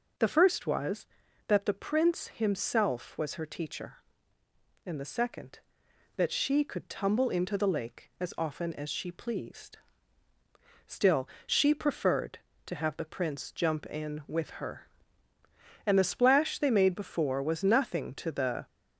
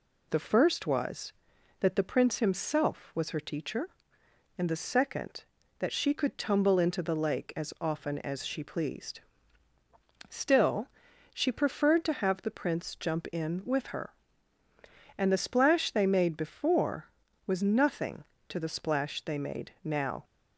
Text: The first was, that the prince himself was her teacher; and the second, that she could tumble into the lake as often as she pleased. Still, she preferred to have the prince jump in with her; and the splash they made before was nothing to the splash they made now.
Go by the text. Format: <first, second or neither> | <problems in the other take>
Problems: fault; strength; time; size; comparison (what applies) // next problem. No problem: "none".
second | stops before "splash they made now"; at 18.6 s